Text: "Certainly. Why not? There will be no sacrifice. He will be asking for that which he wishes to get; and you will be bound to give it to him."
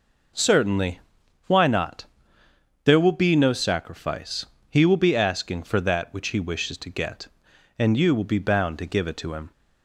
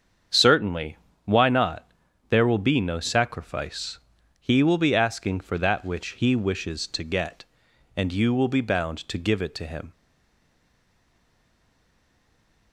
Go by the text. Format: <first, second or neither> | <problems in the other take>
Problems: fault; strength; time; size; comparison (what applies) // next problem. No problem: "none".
first | starts louder than the rest; strong; until 1.6 s; 7.5 dB // stays silent after the last word; strong; from 9.9 s on; 2.8 s long